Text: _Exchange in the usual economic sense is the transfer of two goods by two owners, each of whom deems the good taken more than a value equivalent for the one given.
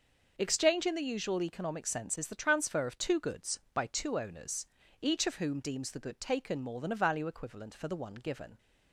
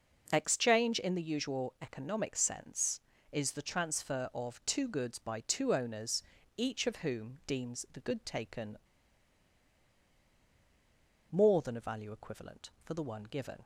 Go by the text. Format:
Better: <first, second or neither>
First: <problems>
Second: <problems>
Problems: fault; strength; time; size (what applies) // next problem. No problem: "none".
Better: first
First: none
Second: pauses between "taken" and "more"; strong; at 8.7 s; 2.5 s long